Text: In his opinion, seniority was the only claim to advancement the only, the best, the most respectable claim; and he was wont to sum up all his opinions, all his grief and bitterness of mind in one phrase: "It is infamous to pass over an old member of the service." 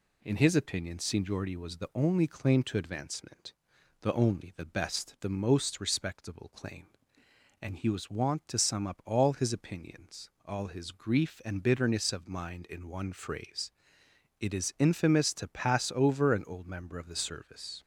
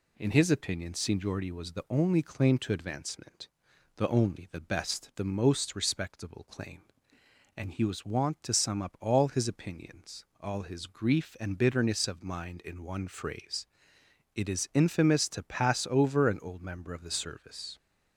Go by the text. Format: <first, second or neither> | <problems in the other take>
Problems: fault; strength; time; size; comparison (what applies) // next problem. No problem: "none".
neither | pauses between "advancement" and "the"; noticeable; the same in both